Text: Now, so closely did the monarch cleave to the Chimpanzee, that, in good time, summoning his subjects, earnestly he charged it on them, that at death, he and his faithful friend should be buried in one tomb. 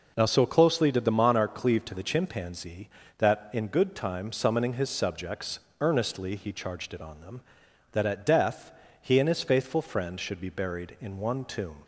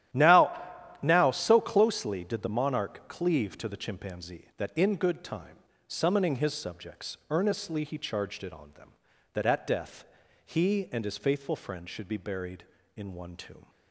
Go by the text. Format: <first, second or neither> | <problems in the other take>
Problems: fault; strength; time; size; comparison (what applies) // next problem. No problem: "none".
first | starts louder than the rest; strong; until 1.5 s; 11.5 dB // says "Now" twice; at 1.0 s